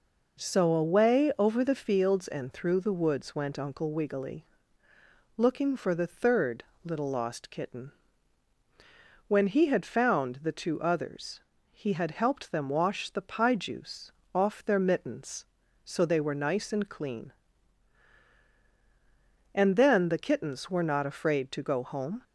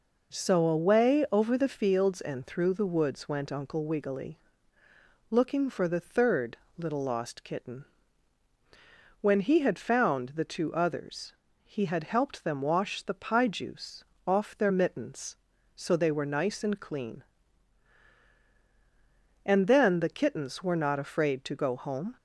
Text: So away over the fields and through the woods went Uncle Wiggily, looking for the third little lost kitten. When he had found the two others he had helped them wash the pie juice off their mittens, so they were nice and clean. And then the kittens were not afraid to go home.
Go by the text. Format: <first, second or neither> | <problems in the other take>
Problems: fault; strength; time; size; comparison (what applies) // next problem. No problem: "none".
neither | pauses between "third" and "little"; slight; the same in both // pauses between "others" and "he"; slight; the same in both // pauses between "juice" and "off"; slight; the same in both